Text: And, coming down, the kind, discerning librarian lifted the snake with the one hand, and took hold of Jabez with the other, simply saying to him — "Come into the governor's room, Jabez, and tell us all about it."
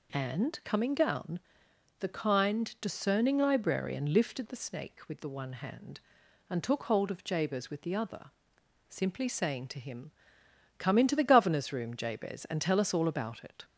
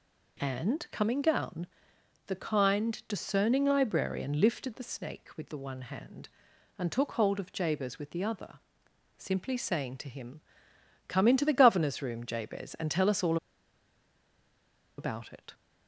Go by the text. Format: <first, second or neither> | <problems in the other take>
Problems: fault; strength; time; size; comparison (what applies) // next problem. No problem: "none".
first | pauses between "all" and "about"; strong; at 13.3 s; 1.6 s long